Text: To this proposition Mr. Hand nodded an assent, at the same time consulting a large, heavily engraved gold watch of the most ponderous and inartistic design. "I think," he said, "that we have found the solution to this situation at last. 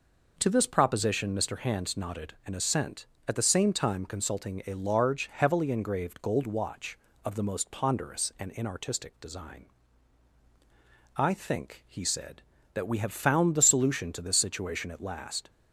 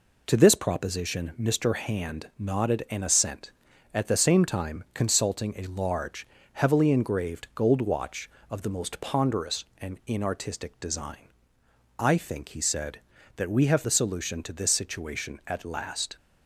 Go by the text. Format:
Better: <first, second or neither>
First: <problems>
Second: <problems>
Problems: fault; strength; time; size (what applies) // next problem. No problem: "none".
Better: first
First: none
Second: skips "found"; at 13.8 s